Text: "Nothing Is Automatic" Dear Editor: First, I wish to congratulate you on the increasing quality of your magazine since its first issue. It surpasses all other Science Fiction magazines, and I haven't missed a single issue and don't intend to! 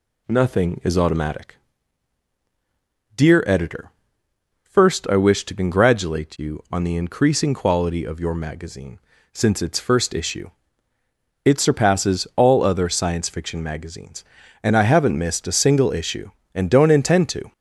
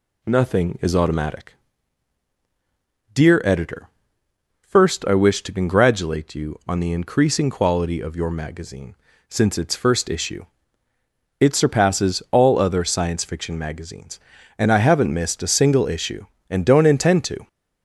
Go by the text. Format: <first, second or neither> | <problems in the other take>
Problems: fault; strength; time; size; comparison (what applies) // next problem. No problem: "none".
neither | pauses between "Automatic" and "Dear"; strong; the same in both // pauses between "magazine" and "since"; slight; the same in both